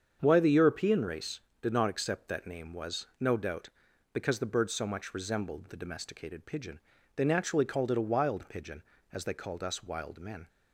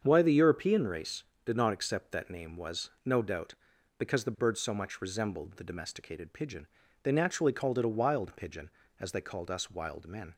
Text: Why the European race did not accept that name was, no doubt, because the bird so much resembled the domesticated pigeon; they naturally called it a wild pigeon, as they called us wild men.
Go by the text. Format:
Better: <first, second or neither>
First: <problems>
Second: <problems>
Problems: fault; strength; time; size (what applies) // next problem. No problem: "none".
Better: neither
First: starts louder than the rest; strong; until 1.2 s; 7.5 dB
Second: starts louder than the rest; strong; until 1.0 s; 7.5 dB